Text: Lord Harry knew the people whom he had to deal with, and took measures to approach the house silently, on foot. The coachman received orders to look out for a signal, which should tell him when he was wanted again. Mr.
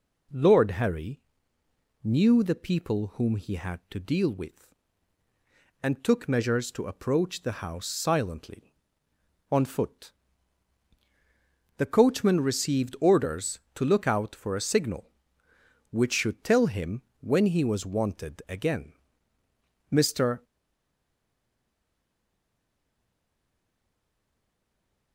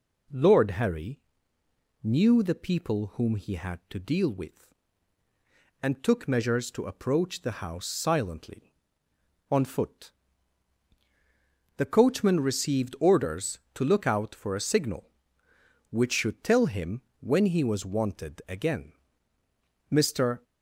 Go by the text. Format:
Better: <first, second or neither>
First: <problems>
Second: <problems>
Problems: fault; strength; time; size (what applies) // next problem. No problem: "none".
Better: second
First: pauses between "Harry" and "knew"; noticeable; at 1.2 s; 0.82 s long // pauses between "him" and "when"; slight; at 17.0 s; 0.20 s long // stays silent after the last word; strong; from 20.4 s on; 4.7 s long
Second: pauses between "Harry" and "knew"; noticeable; at 1.2 s; 0.82 s long // pauses between "him" and "when"; slight; at 17.0 s; 0.20 s long